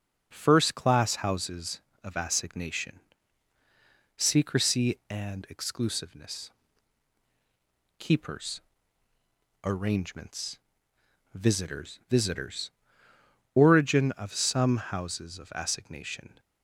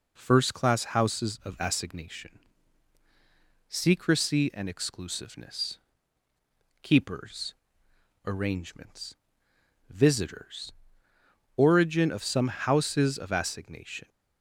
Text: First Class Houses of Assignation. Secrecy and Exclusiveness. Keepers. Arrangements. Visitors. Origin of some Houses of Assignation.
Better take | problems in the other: second | says "Visitors" twice; at 12.0 s

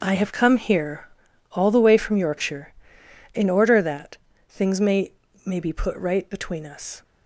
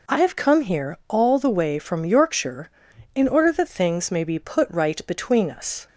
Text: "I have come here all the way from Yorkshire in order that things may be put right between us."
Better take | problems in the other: second | pauses between "here" and "all"; noticeable; at 1.0 s; 0.46 s long // pauses between "that" and "things"; slight; at 4.1 s; 0.32 s long // says "may" twice; at 5.4 s

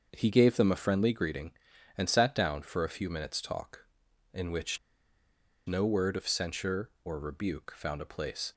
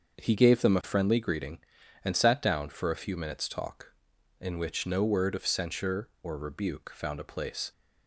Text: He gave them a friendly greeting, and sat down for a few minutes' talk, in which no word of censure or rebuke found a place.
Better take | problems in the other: second | starts louder than the rest; until 1.1 s; 6.5 dB; also in the second // pauses between "which" and "no"; noticeable; at 4.7 s; 0.88 s long

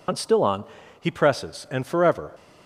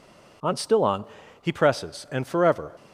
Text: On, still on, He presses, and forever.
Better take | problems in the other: second | loses the start of "On"; at 0.0 s; 65 ms

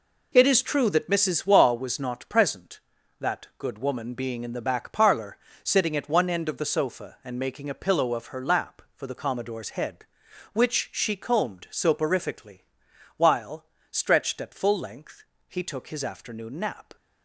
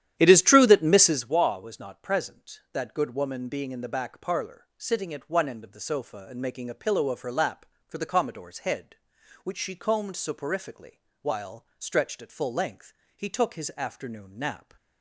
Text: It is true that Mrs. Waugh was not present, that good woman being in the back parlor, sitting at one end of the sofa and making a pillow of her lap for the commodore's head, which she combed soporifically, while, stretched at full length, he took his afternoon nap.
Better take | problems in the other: first | starts louder than the rest; strong; until 1.3 s; 11 dB

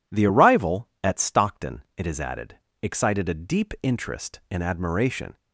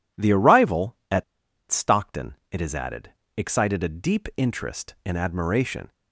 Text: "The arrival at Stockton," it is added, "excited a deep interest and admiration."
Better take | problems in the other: first | pauses between "at" and "Stockton"; noticeable; at 1.2 s; 0.46 s long

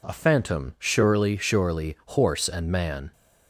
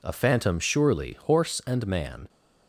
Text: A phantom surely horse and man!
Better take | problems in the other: second | says "surely" twice; at 1.3 s

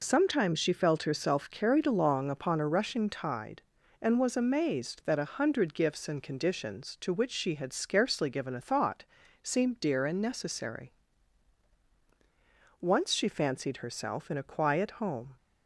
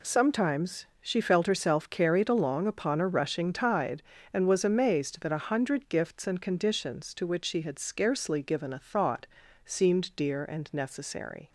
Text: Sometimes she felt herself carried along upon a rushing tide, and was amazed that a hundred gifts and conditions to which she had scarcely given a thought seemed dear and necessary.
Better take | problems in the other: second | pauses between "thought" and "seemed"; at 9.0 s; 0.40 s long; slight in the second // goes on to say "Once she fancied herself in a quiet home"; strong; from 12.8 s on; 2.5 s long

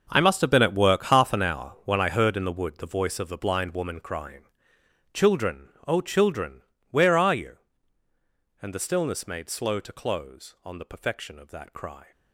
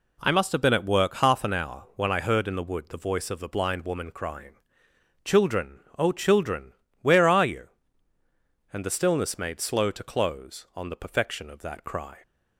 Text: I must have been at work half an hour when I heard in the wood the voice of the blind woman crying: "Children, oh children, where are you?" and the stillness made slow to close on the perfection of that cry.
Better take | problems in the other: second | gets quieter; strong; throughout; 14.5 dB

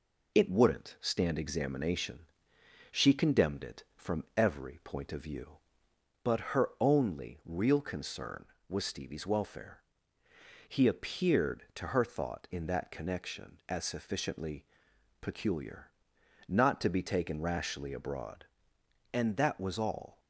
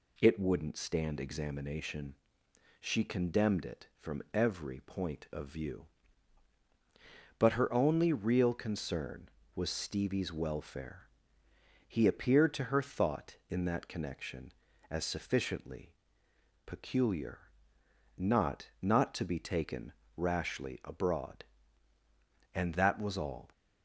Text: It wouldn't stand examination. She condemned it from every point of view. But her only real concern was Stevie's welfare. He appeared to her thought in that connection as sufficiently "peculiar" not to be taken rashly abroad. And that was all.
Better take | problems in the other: first | pauses between "sufficiently" and "peculiar"; noticeable; at 15.9 s; 0.72 s long; noticeable in the first // pauses between "peculiar" and "not"; noticeable; at 17.3 s; 0.78 s long; noticeable in the first // says "not" twice; at 18.8 s // pauses between "taken" and "rashly"; slight; at 19.9 s; 0.22 s long

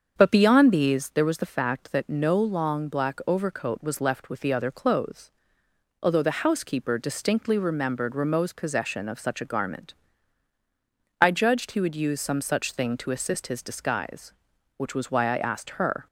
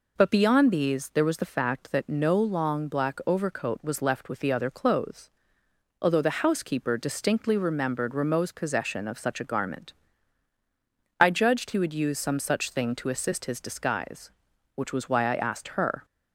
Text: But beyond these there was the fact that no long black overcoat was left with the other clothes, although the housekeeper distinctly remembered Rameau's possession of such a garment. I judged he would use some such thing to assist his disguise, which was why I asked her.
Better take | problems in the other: second | starts louder than the rest; until 1.2 s; 7 dB

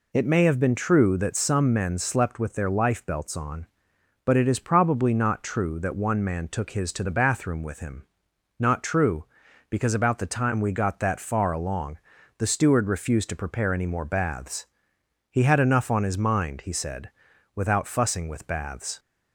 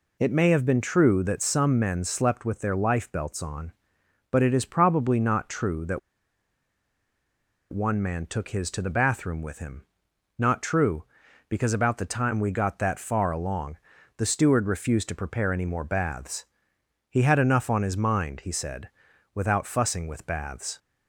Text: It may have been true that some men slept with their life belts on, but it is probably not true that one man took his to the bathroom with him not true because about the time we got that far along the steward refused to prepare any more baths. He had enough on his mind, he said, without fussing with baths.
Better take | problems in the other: first | pauses between "that" and "one"; strong; at 5.9 s; 1.7 s long // pauses between "him" and "not"; noticeable; at 9.8 s; 0.56 s long; noticeable in the first // pauses between "along" and "the"; at 13.7 s; 0.42 s long; also in the first

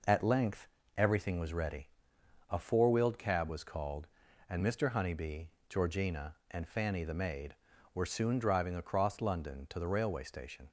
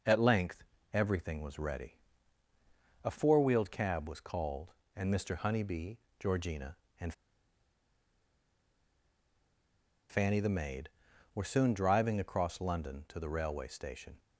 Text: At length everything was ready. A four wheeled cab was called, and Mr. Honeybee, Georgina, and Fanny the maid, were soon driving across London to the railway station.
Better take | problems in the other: first | pauses between "length" and "everything"; slight; at 0.6 s; 0.30 s long; slight in the first // pauses between "and" and "Fanny"; strong; at 7.1 s; 2.9 s long

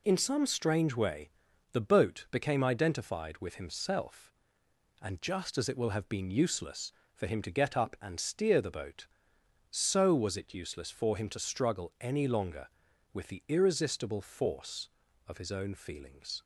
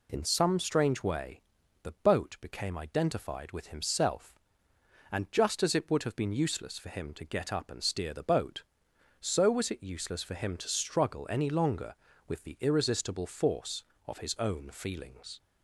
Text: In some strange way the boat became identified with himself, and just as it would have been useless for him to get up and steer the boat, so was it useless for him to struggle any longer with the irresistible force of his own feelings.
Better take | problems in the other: second | pauses between "way" and "the"; at 1.3 s; 0.40 s long; also in the second // says "will" for "would"; at 5.7 s

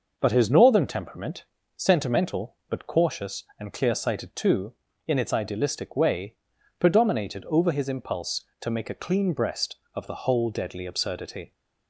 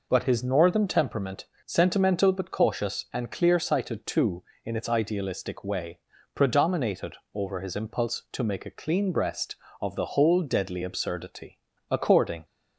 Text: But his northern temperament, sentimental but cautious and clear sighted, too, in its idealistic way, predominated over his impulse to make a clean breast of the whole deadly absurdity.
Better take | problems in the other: first | pauses between "predominated" and "over"; slight; at 7.1 s; 0.18 s long // goes on to say "According"; from 11.8 s on; 0.56 s long

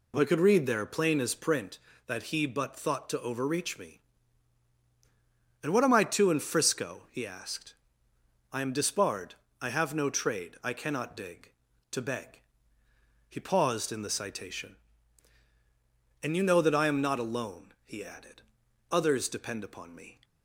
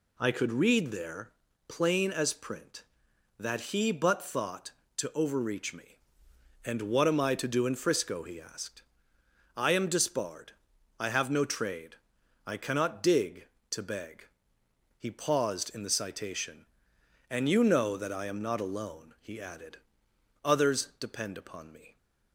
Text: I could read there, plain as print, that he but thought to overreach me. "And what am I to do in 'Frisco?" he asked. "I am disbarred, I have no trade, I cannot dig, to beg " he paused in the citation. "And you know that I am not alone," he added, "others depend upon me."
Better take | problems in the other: second | skips "do"; at 6.3 s

